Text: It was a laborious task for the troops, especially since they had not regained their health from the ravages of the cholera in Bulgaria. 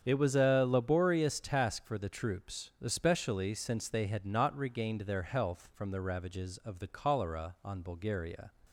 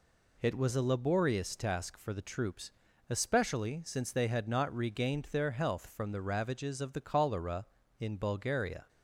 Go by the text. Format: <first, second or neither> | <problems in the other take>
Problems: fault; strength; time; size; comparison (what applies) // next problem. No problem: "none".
second | starts louder than the rest; strong; until 1.0 s; 7.5 dB // says "on" for "in"; at 7.6 s